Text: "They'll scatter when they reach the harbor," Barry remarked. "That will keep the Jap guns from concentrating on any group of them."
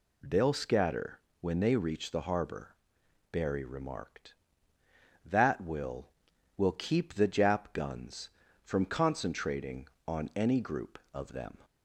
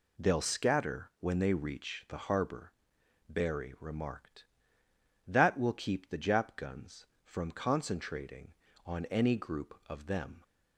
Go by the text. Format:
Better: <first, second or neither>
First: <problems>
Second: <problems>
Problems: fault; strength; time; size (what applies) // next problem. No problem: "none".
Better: second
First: pauses between "scatter" and "when"; slight; at 1.1 s; 0.20 s long // says "will" twice; at 6.5 s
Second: none